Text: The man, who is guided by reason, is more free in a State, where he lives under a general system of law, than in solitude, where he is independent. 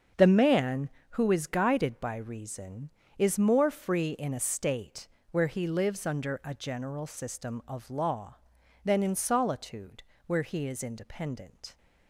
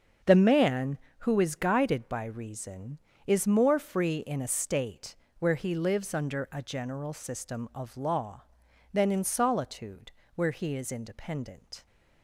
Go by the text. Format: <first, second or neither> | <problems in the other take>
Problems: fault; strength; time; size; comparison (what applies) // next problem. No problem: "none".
neither | starts louder than the rest; the same in both